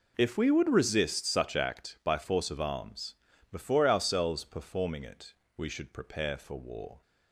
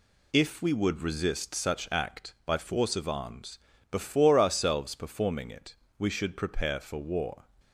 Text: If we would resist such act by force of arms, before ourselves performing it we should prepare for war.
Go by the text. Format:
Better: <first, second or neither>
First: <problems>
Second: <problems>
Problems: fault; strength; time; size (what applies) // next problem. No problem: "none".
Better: neither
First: pauses between "it" and "we"; slight; at 5.3 s; 0.24 s long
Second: pauses between "it" and "we"; slight; at 5.7 s; 0.22 s long